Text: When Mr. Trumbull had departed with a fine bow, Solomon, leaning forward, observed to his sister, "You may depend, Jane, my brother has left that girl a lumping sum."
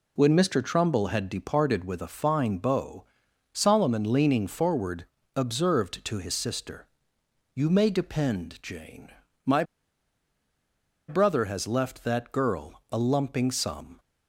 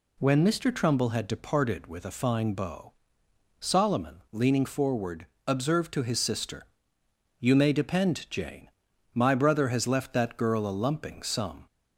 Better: second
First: pauses between "my" and "brother"; strong; at 9.6 s; 1.4 s long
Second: none

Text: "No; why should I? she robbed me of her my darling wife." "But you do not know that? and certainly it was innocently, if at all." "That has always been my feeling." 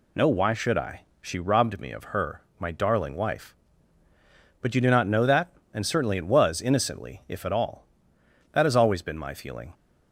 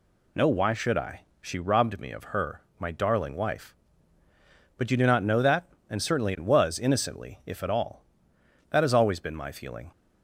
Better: neither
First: pauses between "her" and "my"; slight; at 2.4 s; 0.16 s long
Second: pauses between "her" and "my"; slight; at 2.6 s; 0.16 s long

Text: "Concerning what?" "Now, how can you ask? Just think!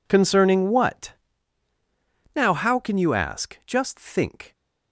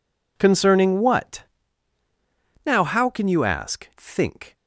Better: first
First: none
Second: skips "Just"; at 3.9 s

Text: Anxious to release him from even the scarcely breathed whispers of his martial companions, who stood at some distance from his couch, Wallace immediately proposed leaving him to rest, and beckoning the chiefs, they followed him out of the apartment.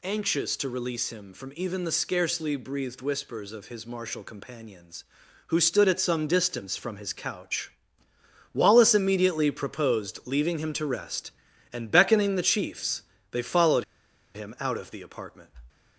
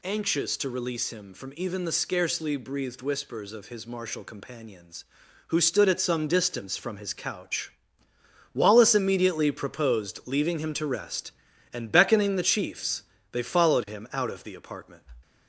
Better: second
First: pauses between "followed" and "him"; noticeable; at 13.8 s; 0.51 s long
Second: none

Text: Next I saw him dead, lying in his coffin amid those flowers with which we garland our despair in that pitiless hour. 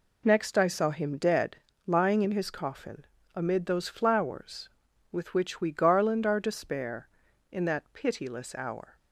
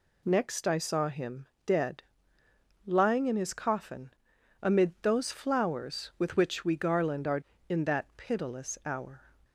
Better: first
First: pauses between "coffin" and "amid"; slight; at 3.0 s; 0.32 s long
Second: pauses between "him" and "dead"; slight; at 1.4 s; 0.18 s long // pauses between "coffin" and "amid"; noticeable; at 4.0 s; 0.52 s long // skips "despair"; at 7.5 s

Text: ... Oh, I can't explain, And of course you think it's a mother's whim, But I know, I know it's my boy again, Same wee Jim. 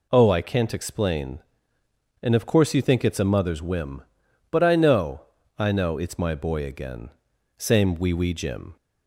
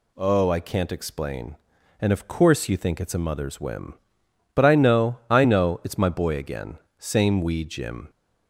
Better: second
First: says "wee" twice; at 8.1 s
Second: none

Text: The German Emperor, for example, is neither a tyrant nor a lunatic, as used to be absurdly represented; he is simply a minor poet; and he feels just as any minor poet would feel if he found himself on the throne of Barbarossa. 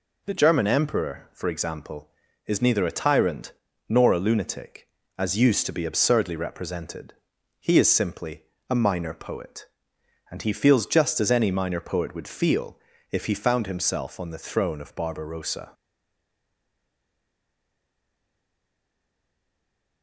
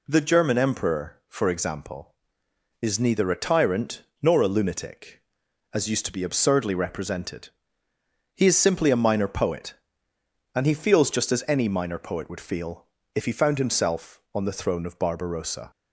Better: second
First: pauses between "tyrant" and "nor"; at 3.5 s; 0.38 s long // pauses between "simply" and "a"; slight; at 8.4 s; 0.26 s long // pauses between "feel" and "if"; slight; at 12.7 s; 0.34 s long // stays silent after the last word; strong; from 15.7 s on; 4.3 s long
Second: pauses between "tyrant" and "nor"; slight; at 4.0 s; 0.18 s long // pauses between "feel" and "if"; slight; at 12.8 s; 0.26 s long

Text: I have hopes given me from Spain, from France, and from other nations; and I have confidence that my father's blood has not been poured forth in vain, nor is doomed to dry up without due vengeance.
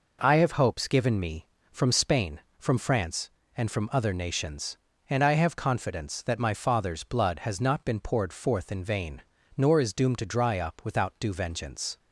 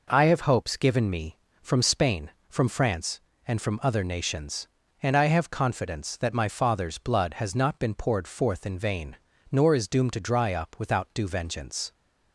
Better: neither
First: none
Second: none

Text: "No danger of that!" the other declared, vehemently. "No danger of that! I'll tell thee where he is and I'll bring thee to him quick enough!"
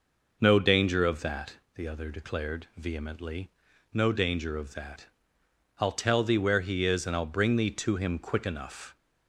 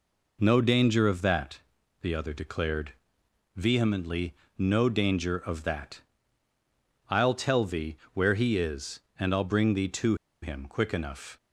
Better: first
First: none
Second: pauses between "thee" and "where"; slight; at 7.9 s; 0.16 s long // pauses between "to" and "him"; slight; at 10.1 s; 0.26 s long

